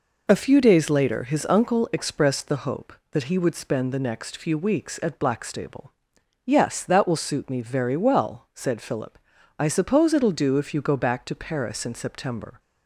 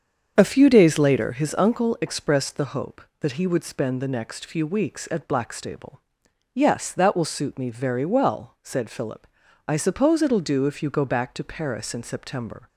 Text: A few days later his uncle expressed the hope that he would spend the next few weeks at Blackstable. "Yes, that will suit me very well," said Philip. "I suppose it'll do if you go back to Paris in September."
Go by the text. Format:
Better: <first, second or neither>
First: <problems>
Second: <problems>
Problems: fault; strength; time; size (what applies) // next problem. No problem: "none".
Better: first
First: none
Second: starts louder than the rest; strong; until 1.5 s; 7.5 dB